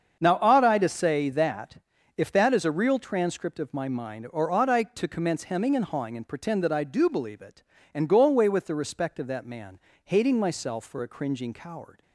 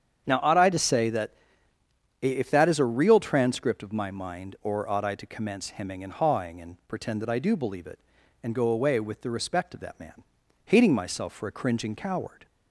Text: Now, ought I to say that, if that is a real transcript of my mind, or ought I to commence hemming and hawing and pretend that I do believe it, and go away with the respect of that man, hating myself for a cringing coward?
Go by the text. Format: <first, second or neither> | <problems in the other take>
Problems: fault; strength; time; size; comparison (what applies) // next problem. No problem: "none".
neither | starts louder than the rest; strong; the same in both